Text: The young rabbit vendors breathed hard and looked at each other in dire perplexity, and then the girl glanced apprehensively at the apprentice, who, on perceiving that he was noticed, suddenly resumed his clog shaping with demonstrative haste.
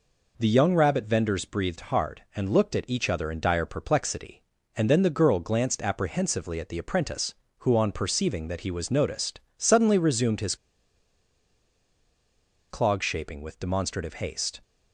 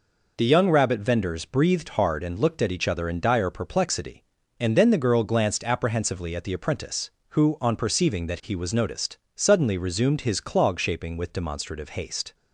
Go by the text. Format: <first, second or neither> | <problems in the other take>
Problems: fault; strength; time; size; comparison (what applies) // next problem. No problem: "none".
second | pauses between "his" and "clog"; strong; at 10.5 s; 2.1 s long